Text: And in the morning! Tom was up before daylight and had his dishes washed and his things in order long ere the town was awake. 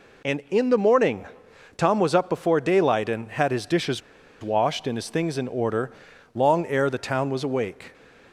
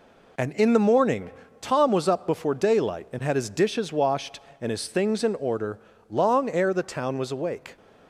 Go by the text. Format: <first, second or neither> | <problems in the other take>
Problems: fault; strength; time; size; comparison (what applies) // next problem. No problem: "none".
second | pauses between "dishes" and "washed"; at 4.0 s; 0.42 s long // pauses between "order" and "long"; noticeable; at 5.8 s; 0.46 s long; slight in the second